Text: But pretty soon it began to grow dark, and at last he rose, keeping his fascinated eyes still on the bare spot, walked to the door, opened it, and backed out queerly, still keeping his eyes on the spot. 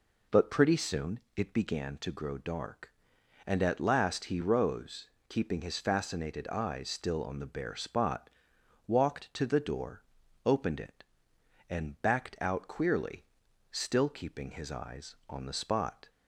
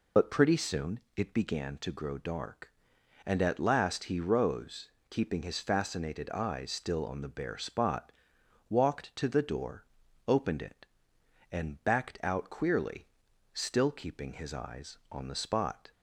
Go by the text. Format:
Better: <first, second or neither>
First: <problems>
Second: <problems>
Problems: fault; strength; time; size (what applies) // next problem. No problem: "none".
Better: first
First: pauses between "soon" and "it"; slight; at 1.1 s; 0.16 s long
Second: loses the start of "But"; at 0.1 s; 60 ms // pauses between "soon" and "it"; slight; at 0.9 s; 0.16 s long